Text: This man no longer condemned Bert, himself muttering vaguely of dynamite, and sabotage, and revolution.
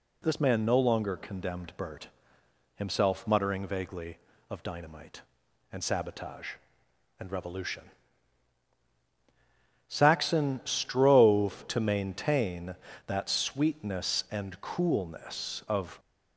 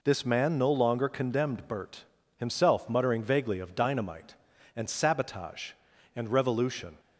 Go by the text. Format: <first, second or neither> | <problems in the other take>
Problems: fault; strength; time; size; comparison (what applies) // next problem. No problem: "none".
second | goes on to say "Saxon strove to maintain that sweetness and coolness of"; strong; from 9.8 s on; 6.1 s long